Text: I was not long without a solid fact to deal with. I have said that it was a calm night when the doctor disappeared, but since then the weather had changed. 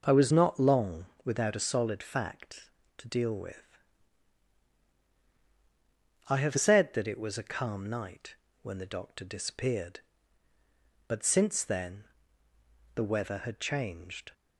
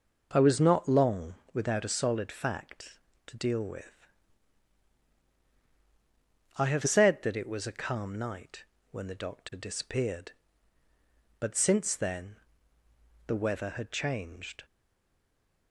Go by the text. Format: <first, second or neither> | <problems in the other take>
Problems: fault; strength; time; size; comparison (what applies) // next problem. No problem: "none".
first | pauses between "long" and "without"; slight; at 1.3 s; 0.18 s long; slight in the first // pauses between "night" and "when"; slight; at 8.6 s; 0.28 s long; slight in the first // pauses between "then" and "the"; noticeable; at 12.3 s; 0.92 s long; noticeable in the first // stays silent after the last word; from 14.6 s on; 1.1 s long